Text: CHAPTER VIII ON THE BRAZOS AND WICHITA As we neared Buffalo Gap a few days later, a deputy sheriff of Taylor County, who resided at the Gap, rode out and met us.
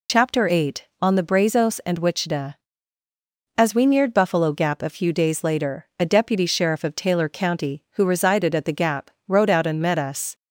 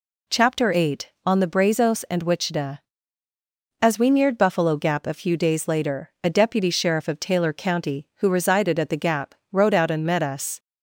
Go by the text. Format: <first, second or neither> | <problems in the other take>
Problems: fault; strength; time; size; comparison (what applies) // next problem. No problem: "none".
second | loses the start of "CHAPTER"; at 0.0 s; 50 ms